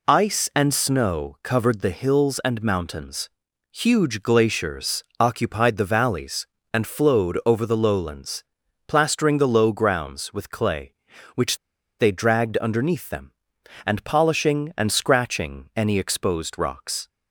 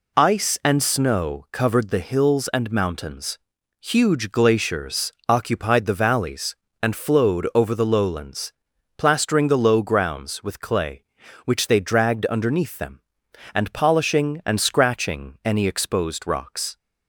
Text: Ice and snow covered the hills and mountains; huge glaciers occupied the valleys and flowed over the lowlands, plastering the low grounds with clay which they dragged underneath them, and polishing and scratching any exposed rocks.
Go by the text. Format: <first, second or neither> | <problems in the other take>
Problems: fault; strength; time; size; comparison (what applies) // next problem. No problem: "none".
second | pauses between "glaciers" and "occupied"; slight; at 5.0 s; 0.16 s long; slight in the second // pauses between "which" and "they"; at 11.5 s; 0.42 s long